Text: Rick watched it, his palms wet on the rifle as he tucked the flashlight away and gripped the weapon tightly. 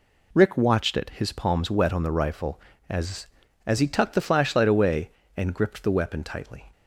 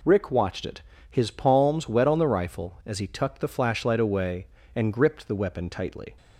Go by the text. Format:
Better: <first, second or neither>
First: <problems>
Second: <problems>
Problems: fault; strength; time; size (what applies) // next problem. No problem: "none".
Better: second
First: says "as" twice; at 3.6 s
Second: none